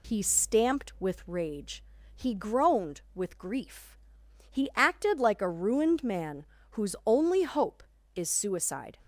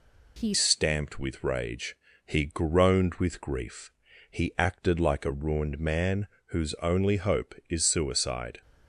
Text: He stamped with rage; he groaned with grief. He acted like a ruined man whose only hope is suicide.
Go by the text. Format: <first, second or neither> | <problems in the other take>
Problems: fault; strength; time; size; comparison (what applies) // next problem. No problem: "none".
first | changes voice at "stamped"; from 0.5 s on; 8.1 s long // pauses between "man" and "whose"; slight; at 6.2 s; 0.22 s long; slight in the first